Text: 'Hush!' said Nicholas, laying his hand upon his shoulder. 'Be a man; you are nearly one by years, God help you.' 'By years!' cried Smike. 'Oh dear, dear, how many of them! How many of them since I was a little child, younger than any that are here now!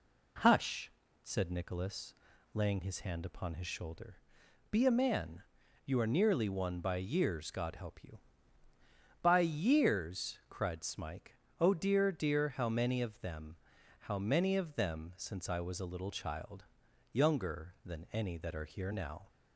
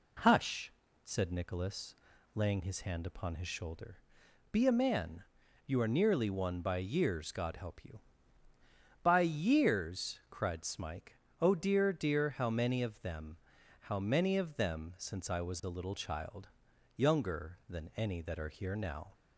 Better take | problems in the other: neither | none

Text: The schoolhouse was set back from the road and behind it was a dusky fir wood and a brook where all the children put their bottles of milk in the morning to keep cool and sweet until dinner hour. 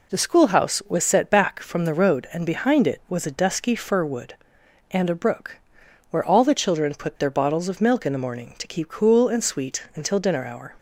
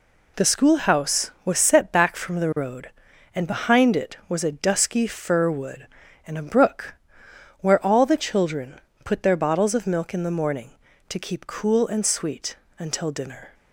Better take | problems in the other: first | pauses between "brook" and "where"; noticeable; at 6.9 s; 0.66 s long; noticeable in the first // pauses between "children" and "put"; slight; at 8.7 s; 0.24 s long // pauses between "sweet" and "until"; slight; at 12.5 s; 0.22 s long // stops before "hour"; at 13.5 s

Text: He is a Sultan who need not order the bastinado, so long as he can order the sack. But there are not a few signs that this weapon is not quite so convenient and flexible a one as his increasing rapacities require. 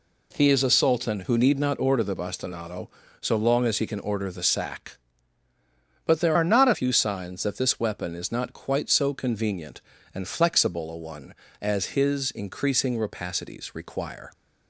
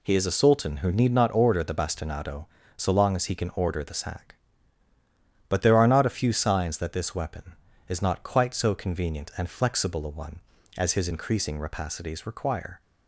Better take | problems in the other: second | changes voice from "are" to "a"; from 6.3 to 6.7 s; 0.4 s long

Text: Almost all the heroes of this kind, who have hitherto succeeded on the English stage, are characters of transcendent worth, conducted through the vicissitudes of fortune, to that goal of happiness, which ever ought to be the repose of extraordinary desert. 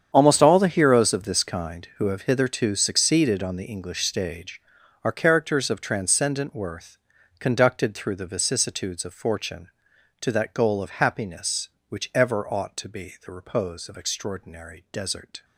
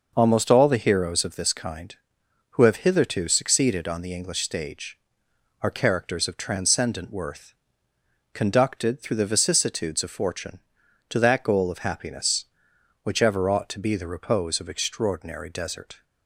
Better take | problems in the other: second | gets quieter; strong; throughout; 14.5 dB

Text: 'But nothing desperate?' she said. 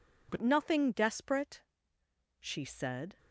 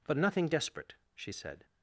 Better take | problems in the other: second | changes voice at "nothing"; from 0.3 s on; 2.8 s long

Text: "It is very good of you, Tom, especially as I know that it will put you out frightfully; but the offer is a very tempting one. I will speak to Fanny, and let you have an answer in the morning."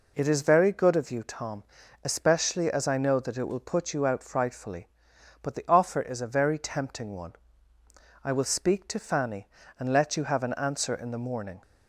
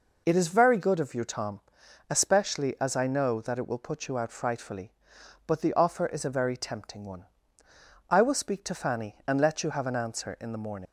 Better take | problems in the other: first | leaves "morning" unfinished; at 10.8 s; 115 ms

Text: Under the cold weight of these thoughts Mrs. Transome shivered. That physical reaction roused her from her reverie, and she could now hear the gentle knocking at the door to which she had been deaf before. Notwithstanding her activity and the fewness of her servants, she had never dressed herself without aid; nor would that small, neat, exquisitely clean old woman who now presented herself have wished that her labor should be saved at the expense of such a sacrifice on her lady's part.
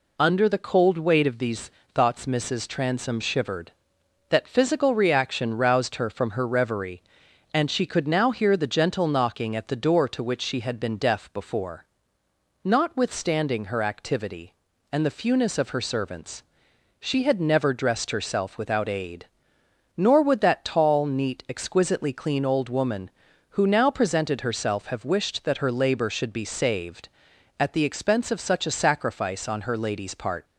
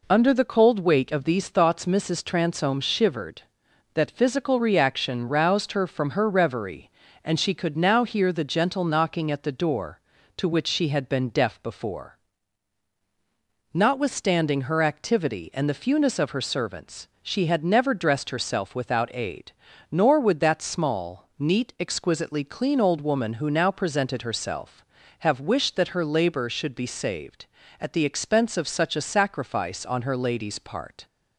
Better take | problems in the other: second | pauses between "these" and "thoughts"; slight; at 1.7 s; 0.20 s long // says "tall" for "small"; at 20.6 s

